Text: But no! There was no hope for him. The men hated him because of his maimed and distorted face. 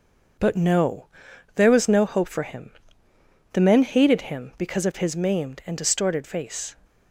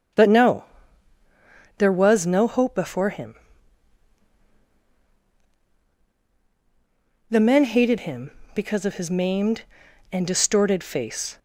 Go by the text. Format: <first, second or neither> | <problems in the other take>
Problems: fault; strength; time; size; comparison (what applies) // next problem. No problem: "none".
first | starts louder than the rest; strong; until 2.2 s; 8 dB // says "before" for "for"; at 2.7 s